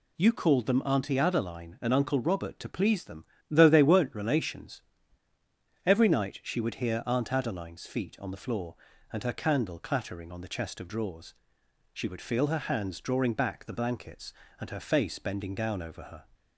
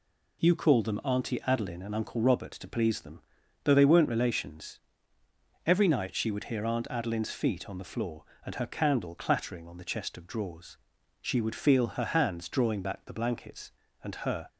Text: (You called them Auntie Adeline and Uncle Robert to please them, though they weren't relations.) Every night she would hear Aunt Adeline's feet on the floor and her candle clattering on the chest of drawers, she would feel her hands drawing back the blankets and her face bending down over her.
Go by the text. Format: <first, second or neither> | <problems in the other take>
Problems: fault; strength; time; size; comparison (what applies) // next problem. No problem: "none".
first | stops before "face bending down over her"; at 14.4 s